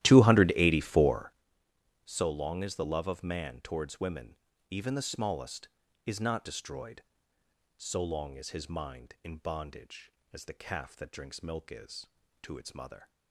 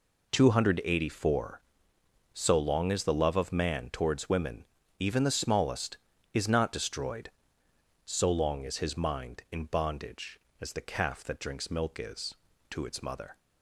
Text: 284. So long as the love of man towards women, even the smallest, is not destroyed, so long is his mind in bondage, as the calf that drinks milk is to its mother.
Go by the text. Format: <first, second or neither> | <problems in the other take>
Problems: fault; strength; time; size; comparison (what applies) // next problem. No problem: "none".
second | starts louder than the rest; strong; until 1.4 s; 14 dB